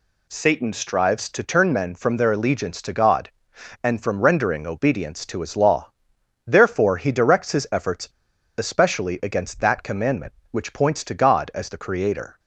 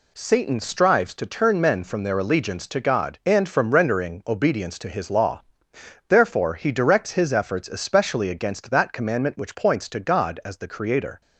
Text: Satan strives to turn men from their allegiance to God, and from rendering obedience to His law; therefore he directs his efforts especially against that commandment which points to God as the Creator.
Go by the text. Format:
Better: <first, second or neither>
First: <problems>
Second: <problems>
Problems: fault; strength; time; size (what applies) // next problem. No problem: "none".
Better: second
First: pauses between "efforts" and "especially"; noticeable; at 8.0 s; 0.47 s long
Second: none